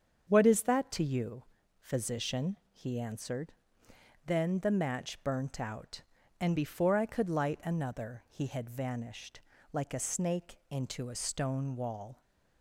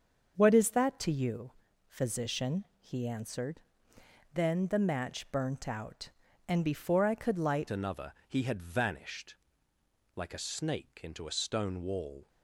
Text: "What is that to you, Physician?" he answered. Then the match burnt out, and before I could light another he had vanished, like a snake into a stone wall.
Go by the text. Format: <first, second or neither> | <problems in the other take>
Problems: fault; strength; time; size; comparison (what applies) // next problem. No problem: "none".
first | starts louder than the rest; until 1.3 s; 6.5 dB; strong in the first // changes voice at "another"; from 7.7 s on; 4.5 s long // pauses between "another" and "he"; slight; at 8.1 s; 0.16 s long